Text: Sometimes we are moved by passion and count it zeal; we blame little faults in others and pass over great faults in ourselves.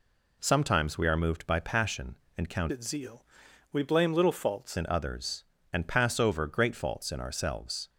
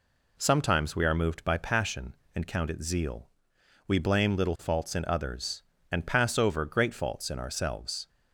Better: second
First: changes voice from "it" to "faults"; from 2.7 to 4.7 s; 2.0 s long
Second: none

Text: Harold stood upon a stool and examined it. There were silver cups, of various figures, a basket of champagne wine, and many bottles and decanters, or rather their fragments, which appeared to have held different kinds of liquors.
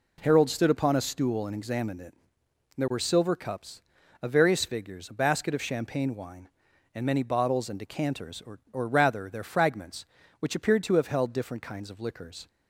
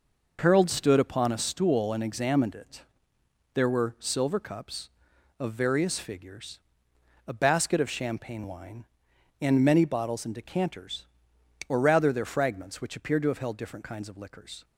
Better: second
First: says "or" twice; at 8.7 s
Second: none

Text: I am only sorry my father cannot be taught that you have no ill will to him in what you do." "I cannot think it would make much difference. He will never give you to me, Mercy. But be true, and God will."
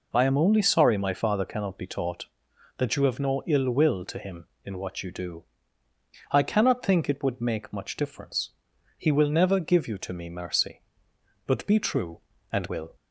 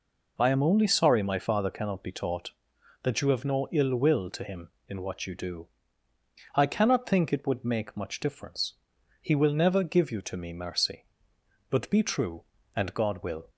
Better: second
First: skips "God"; at 12.6 s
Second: none

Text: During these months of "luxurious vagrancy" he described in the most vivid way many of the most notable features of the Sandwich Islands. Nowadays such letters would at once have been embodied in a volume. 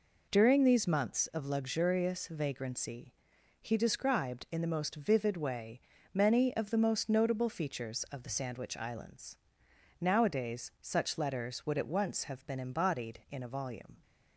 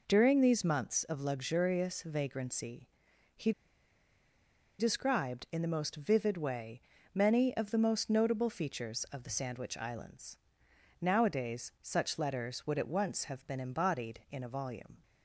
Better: first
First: pauses between "vagrancy" and "he"; noticeable; at 3.1 s; 0.46 s long // pauses between "way" and "many"; slight; at 5.7 s; 0.34 s long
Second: pauses between "vagrancy" and "he"; noticeable; at 2.8 s; 0.46 s long // pauses between "he" and "described"; strong; at 3.5 s; 1.2 s long // pauses between "way" and "many"; slight; at 6.8 s; 0.34 s long

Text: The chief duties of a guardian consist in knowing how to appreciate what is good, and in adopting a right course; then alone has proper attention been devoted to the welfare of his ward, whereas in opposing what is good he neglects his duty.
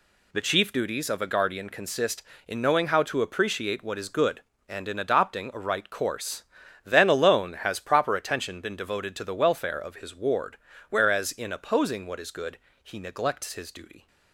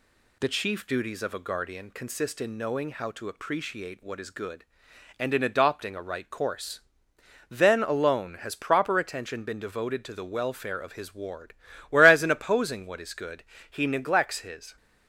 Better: first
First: pauses between "good" and "he"; slight; at 12.5 s; 0.24 s long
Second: pauses between "good" and "he"; slight; at 13.4 s; 0.26 s long // stops before "duty"; at 14.7 s

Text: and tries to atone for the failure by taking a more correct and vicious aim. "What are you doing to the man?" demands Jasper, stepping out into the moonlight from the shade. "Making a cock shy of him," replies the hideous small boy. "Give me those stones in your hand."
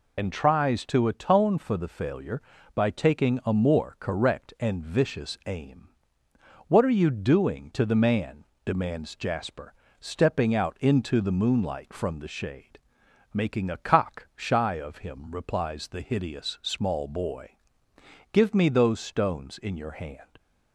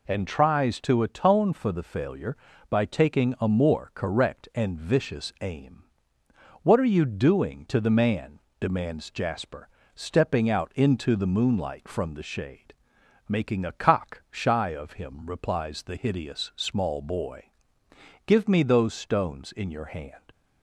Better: second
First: loses the start of "and"; at 0.1 s; 70 ms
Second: none

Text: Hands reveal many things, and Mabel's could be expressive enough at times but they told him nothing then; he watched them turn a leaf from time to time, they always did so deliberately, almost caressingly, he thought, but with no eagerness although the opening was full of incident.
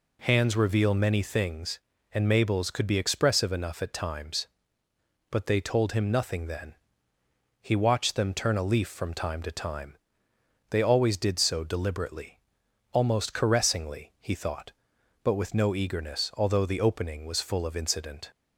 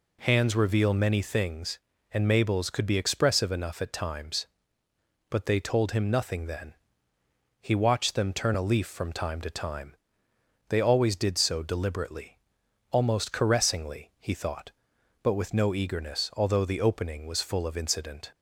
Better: neither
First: none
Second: none

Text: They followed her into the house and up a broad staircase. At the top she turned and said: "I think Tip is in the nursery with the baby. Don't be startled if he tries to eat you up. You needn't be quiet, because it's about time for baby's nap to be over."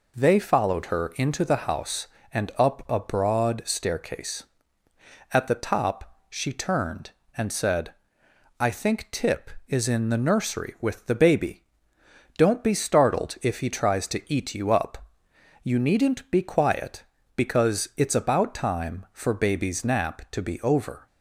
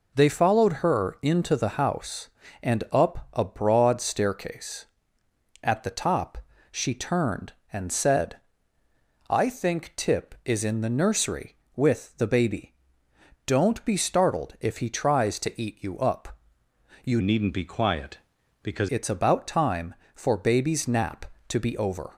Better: first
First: none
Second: pauses between "top" and "she"; slight; at 6.3 s; 0.32 s long // changes voice from "needn't" to "because"; from 17.2 to 18.8 s; 1.6 s long

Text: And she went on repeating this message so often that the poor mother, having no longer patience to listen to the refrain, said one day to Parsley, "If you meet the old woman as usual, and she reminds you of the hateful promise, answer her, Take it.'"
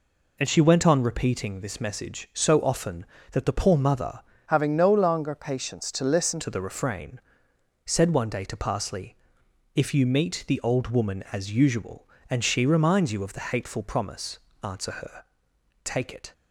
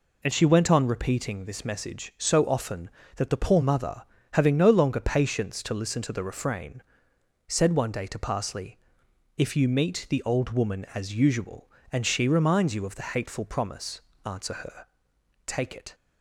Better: second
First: changes voice from "having" to "listen"; from 4.4 to 6.4 s; 2.0 s long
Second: none

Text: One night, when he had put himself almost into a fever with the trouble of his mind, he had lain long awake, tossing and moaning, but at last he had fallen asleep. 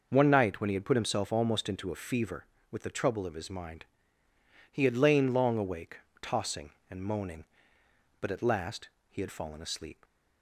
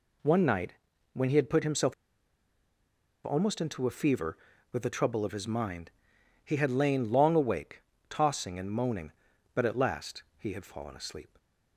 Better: first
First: pauses between "last" and "he"; slight; at 8.8 s; 0.20 s long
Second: pauses between "himself" and "almost"; strong; at 1.9 s; 1.3 s long // pauses between "last" and "he"; slight; at 10.2 s; 0.16 s long

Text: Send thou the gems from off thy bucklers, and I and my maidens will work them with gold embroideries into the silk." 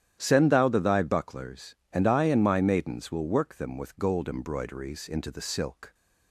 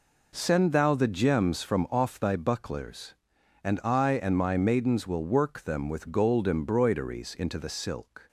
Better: second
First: starts louder than the rest; strong; until 1.2 s; 10.5 dB // skips "gems from off"; at 0.7 s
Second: none

